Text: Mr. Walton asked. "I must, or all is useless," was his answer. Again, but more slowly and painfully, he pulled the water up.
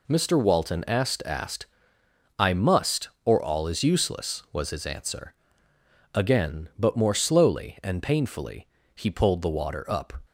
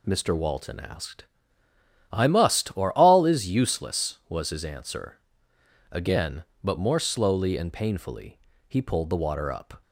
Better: second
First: says "asked" twice; at 1.2 s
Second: none

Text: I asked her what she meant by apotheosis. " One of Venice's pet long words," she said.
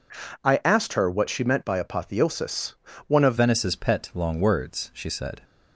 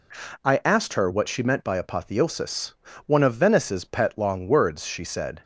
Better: second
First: changes voice at "Venice's"; from 3.3 s on; 2.1 s long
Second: none

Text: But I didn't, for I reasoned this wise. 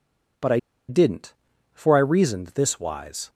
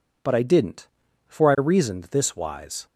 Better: second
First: pauses between "I" and "didn't"; slight; at 0.5 s; 0.30 s long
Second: none

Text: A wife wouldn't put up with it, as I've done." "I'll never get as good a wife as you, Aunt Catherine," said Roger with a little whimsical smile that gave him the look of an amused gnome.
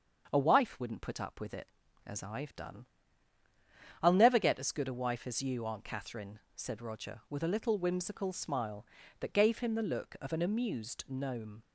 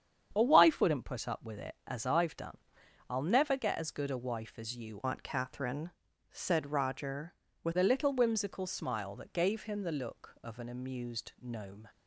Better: first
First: starts louder than the rest; until 1.3 s; 6.5 dB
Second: starts louder than the rest; strong; until 1.3 s; 8.5 dB // changes voice from "Aunt" to "with"; from 5.0 to 7.7 s; 2.7 s long

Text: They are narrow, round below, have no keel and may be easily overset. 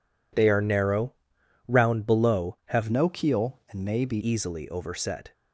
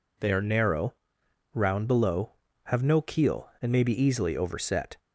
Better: second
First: changes voice from "no" to "be"; from 2.9 to 4.1 s; 1.2 s long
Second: none

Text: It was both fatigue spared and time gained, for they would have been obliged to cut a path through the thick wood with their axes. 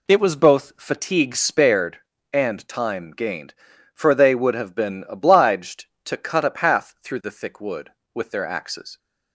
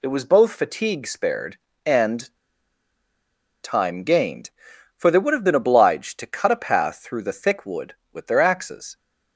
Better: first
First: none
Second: pauses between "and" and "time"; strong; at 2.3 s; 1.2 s long

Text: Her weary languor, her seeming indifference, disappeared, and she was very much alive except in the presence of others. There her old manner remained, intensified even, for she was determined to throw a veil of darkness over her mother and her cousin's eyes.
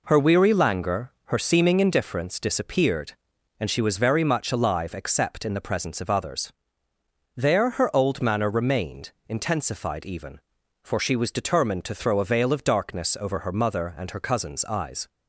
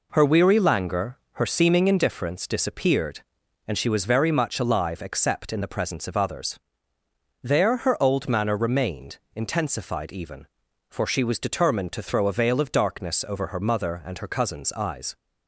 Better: neither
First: none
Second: none

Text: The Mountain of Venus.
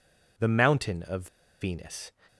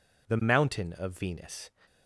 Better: second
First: pauses between "of" and "Venus"; slight; at 1.2 s; 0.34 s long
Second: none

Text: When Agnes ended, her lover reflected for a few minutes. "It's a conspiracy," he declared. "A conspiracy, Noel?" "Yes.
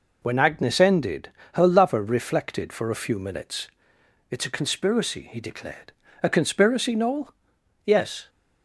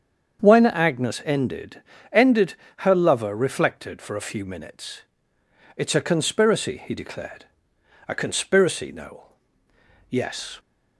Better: first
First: none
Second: starts louder than the rest; strong; until 1.4 s; 7.5 dB // says "ended" twice; at 2.1 s

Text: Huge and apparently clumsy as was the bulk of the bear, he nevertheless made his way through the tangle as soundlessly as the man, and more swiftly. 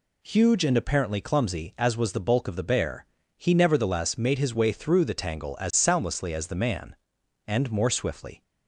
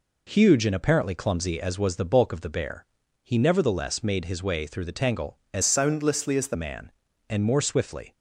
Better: first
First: none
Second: changes voice from "soundlessly" to "the"; from 5.6 to 6.5 s; 0.9 s long

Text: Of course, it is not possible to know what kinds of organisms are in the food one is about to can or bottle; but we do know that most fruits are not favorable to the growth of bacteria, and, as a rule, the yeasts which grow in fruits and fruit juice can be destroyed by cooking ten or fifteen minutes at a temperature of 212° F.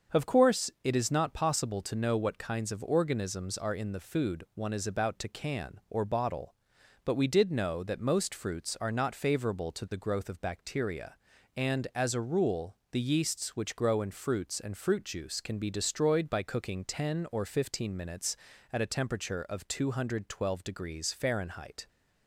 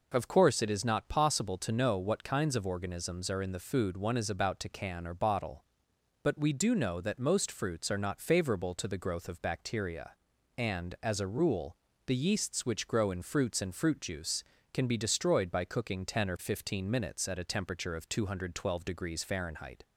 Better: second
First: starts louder than the rest; until 1.2 s; 7 dB // says "did" for "do"; at 7.2 s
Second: none

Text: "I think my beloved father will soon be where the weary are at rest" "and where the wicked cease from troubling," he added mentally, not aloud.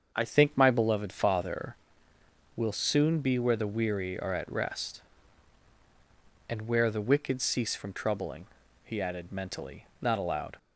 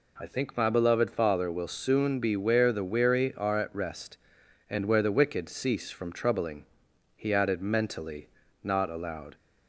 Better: second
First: starts louder than the rest; until 1.2 s; 7 dB // changes voice at "think"; from 0.2 s on; 10.3 s long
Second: none

